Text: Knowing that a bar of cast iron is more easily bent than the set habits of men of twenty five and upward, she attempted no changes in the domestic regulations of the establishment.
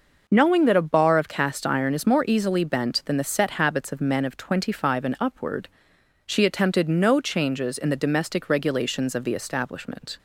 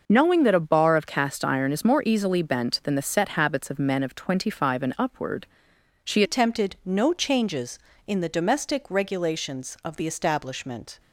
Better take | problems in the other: first | changes voice at "attempted"; from 6.2 s on; 4.7 s long

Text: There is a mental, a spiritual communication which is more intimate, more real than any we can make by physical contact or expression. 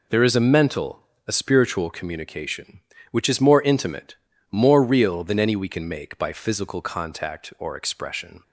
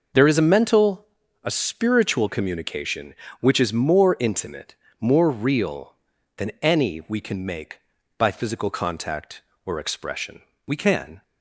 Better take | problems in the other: first | goes on to say "We can"; from 10.6 s on; 0.56 s long

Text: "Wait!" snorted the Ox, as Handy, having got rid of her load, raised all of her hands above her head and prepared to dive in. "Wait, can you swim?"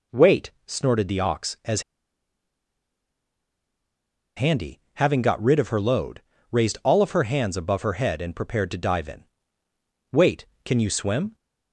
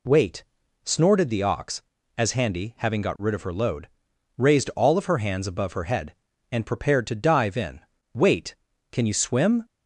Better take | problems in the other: second | pauses between "as" and "Handy"; strong; at 1.8 s; 2.5 s long

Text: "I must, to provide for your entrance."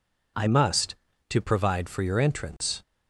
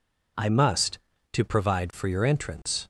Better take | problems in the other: neither | none

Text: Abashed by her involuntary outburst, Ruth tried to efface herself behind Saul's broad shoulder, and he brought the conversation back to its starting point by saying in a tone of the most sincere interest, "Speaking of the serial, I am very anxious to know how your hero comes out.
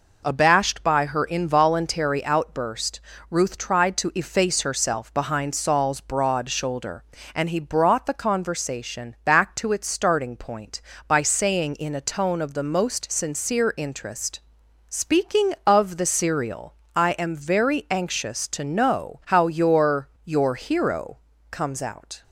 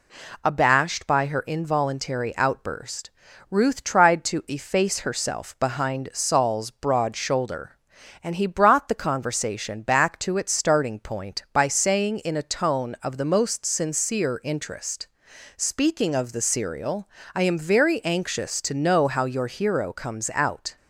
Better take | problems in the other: second | says "your" twice; at 20.2 s // pauses between "hero" and "comes"; slight; at 21.1 s; 0.34 s long

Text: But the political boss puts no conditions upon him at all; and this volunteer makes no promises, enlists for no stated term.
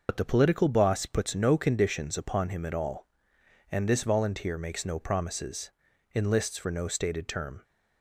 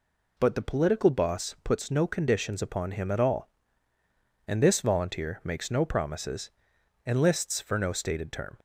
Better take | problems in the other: second | loses the start of "But"; at 0.0 s; 60 ms

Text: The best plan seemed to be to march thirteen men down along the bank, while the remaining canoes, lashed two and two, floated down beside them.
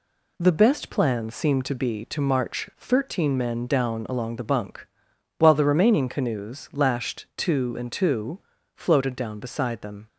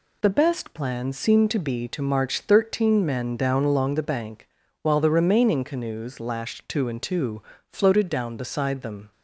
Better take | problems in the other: second | says "bunk" for "bank"; at 4.4 s

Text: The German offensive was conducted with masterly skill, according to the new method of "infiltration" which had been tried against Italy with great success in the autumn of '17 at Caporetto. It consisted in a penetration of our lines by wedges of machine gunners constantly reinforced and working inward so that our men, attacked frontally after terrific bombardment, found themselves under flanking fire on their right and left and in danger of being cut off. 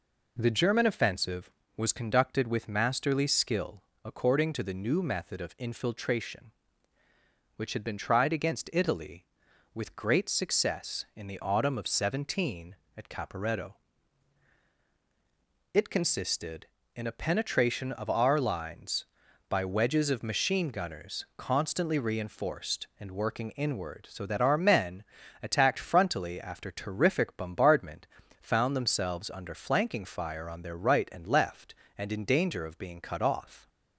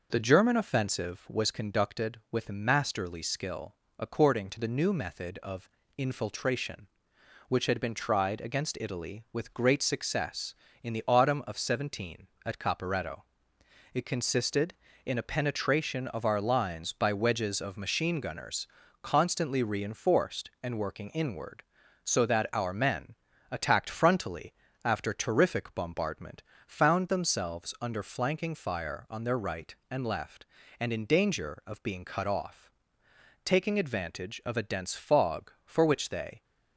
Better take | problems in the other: first | pauses between "of" and "infiltration"; slight; at 5.6 s; 0.28 s long // pauses between "gunners" and "constantly"; slight; at 18.6 s; 0.36 s long // pauses between "frontally" and "after"; slight; at 24.5 s; 0.30 s long // goes on to say "Taking advantage of a dense fog for which they"; strong; from 33.4 s on; 3.0 s long

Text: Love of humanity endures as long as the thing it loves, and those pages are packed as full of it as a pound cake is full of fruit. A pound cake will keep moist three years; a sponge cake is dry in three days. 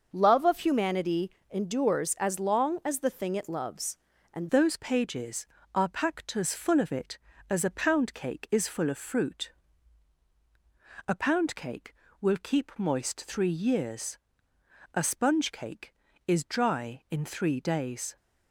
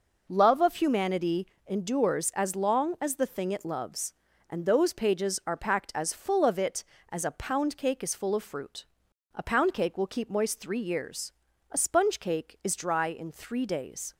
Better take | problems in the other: second | starts louder than the rest; until 1.1 s; 6.5 dB // pauses between "humanity" and "endures"; slight; at 1.2 s; 0.20 s long; slight in the second // changes voice at "those"; from 4.4 s on; 13.7 s long

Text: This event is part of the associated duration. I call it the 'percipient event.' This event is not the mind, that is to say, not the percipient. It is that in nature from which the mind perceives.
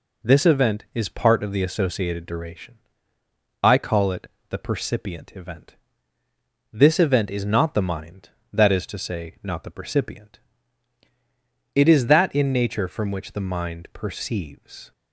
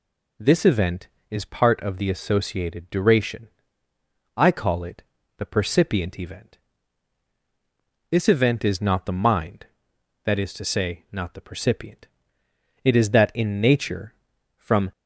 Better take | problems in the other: first | pauses between "it" and "the"; slight; at 5.0 s; 0.36 s long; slight in the first // stops before "which the mind perceives"; at 14.9 s

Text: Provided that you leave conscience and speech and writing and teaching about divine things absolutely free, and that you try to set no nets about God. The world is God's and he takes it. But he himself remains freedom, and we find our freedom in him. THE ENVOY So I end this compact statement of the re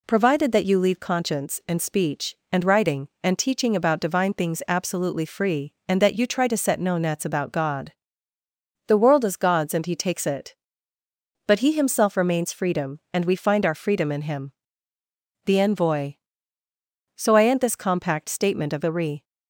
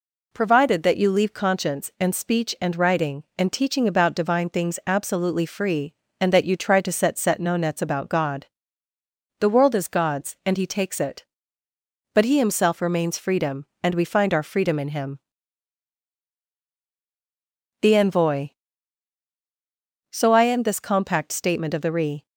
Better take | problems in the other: first | says "set" twice; at 7.1 s

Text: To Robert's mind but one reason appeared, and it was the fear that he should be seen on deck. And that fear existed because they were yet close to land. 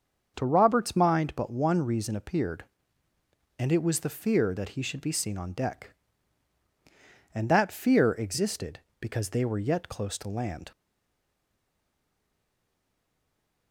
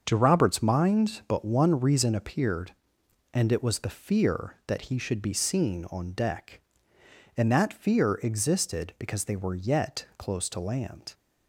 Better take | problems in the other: second | starts louder than the rest; until 1.3 s; 7 dB; also in the second // stays silent after the last word; strong; from 10.7 s on; 3.0 s long

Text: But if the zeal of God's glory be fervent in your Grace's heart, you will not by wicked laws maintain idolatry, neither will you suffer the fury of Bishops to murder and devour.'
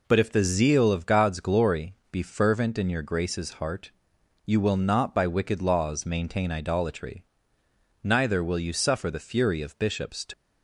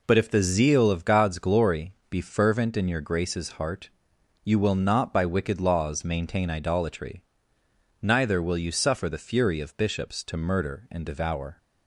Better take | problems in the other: second | pauses between "glory" and "be"; slight; at 1.9 s; 0.16 s long; slight in the second // stops before "murder and devour"; at 10.3 s

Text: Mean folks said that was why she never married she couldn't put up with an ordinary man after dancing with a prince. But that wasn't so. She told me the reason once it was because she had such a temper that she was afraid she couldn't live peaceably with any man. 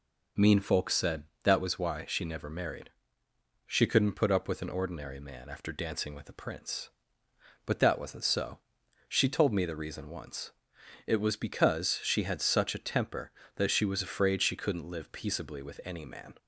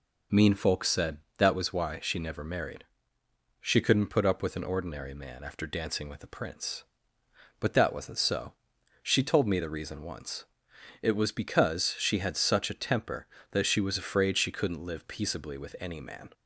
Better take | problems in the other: neither | pauses between "married" and "she"; noticeable; the same in both // pauses between "once" and "it"; noticeable; the same in both

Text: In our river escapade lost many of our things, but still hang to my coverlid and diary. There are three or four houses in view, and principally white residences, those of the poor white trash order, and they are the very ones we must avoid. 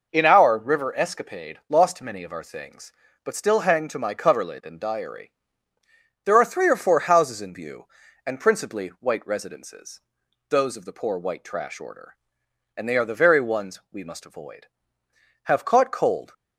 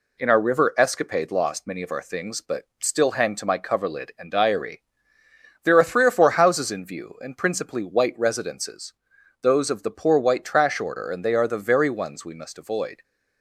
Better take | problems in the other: second | goes on to say "Have caught cold"; noticeable; from 15.4 s on; 0.90 s long

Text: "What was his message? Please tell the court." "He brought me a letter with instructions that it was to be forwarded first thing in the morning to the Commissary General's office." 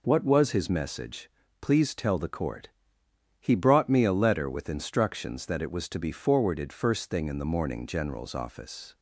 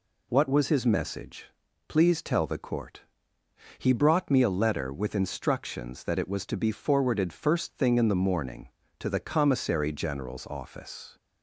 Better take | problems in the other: second | skips "to the Commissary"; at 7.8 s

